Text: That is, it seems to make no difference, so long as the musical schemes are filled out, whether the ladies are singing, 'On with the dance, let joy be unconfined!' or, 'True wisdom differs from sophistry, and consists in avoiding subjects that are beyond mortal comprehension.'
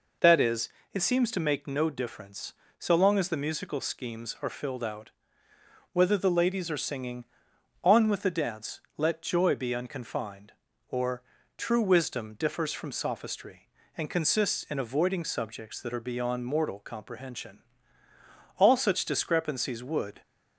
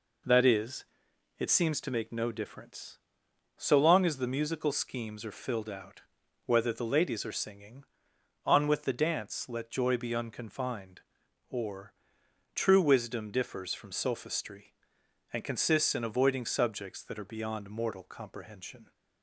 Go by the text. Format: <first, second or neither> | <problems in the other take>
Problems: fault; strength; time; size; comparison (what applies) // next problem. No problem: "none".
second | goes on to say "All such discrepancies would"; from 18.5 s on; 1.6 s long